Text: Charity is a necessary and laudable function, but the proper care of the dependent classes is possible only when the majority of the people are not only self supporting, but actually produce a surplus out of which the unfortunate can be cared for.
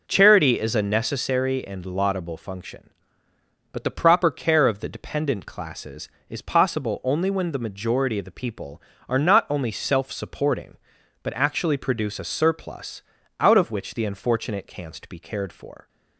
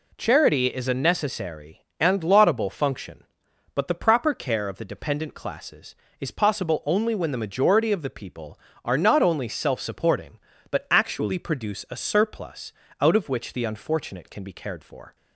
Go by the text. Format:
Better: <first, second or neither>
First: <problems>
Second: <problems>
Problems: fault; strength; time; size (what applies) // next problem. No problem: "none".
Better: second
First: pauses between "surplus" and "out"; at 13.0 s; 0.38 s long // says "canst" for "can"; at 14.6 s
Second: pauses between "surplus" and "out"; slight; at 12.7 s; 0.28 s long